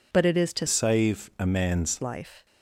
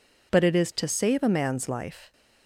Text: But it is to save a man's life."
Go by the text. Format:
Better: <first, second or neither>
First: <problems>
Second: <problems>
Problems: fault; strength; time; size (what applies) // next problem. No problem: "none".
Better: second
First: changes voice from "save" to "man's"; from 0.6 to 1.9 s; 1.3 s long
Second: none